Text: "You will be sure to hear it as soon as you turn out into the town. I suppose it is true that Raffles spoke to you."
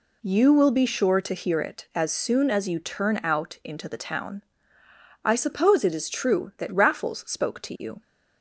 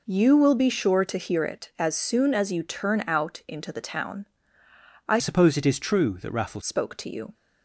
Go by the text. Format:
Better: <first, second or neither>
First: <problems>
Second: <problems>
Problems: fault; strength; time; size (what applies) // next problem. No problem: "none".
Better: first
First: none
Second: changes voice from "suppose" to "Raffles"; from 5.1 to 6.6 s; 1.5 s long